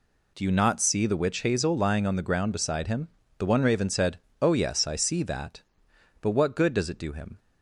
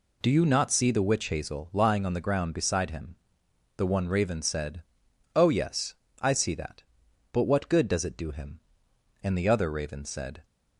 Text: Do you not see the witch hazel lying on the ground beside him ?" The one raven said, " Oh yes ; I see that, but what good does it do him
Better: first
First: none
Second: goes on to say "And the other raven said"; noticeable; from 9.2 s on; 1.2 s long

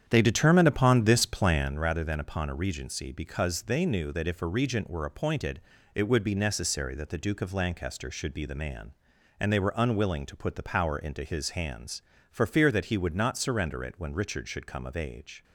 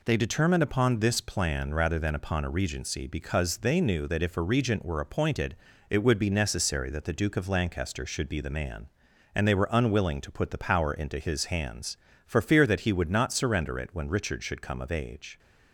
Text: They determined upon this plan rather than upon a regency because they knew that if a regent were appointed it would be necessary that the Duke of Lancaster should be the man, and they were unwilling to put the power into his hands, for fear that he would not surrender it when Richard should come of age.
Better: second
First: starts louder than the rest; strong; until 1.8 s; 9 dB // pauses between "appointed" and "it"; slight; at 5.5 s; 0.36 s long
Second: pauses between "appointed" and "it"; slight; at 5.5 s; 0.36 s long

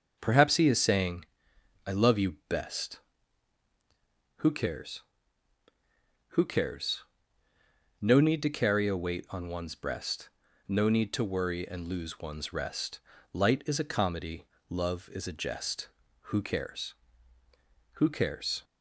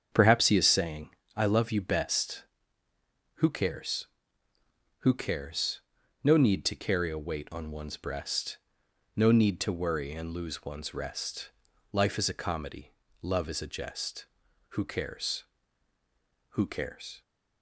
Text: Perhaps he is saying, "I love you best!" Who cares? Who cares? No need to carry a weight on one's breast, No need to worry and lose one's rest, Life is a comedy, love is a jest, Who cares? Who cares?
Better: second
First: starts louder than the rest; until 1.2 s; 6.5 dB // says "Light" for "Life"; at 13.3 s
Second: starts louder than the rest; strong; until 1.1 s; 7.5 dB

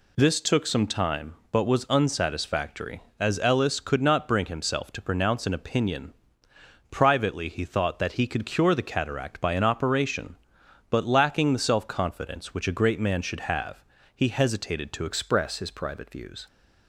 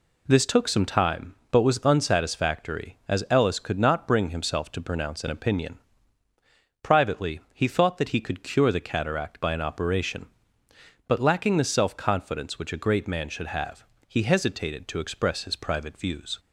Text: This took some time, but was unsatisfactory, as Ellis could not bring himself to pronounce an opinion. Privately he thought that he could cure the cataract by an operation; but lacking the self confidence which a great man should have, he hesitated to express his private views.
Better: second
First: changes voice at "express"; from 15.0 s on; 1.4 s long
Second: none

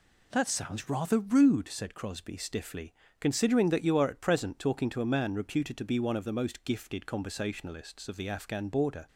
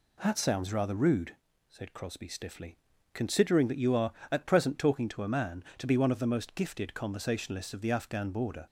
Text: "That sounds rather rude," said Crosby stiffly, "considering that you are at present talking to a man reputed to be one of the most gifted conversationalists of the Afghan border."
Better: first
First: none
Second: skips "reputed"; at 5.7 s

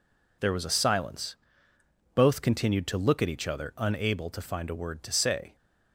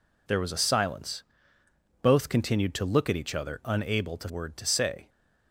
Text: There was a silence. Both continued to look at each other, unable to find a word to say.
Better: first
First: none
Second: skips "find a"; at 4.2 s

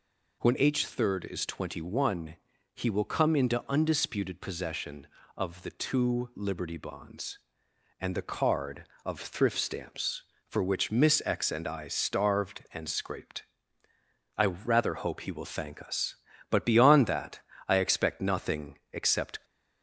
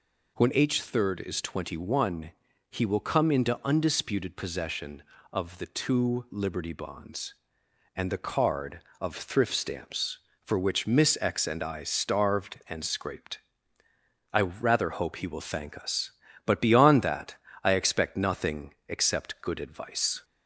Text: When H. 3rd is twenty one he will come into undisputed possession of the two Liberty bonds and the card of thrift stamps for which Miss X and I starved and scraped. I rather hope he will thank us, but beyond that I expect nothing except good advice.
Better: second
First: pauses between "one" and "he"; slight; at 2.3 s; 0.36 s long // pauses between "that" and "I"; slight; at 17.4 s; 0.26 s long // stops before "good advice"; at 19.4 s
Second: pauses between "one" and "he"; slight; at 2.3 s; 0.36 s long // pauses between "that" and "I"; slight; at 17.3 s; 0.26 s long

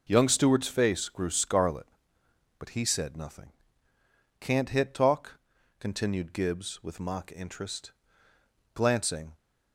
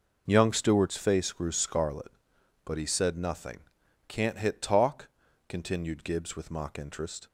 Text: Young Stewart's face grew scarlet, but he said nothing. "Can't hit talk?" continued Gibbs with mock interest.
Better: second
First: goes on to say "Glancing"; from 8.7 s on; 0.60 s long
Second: none

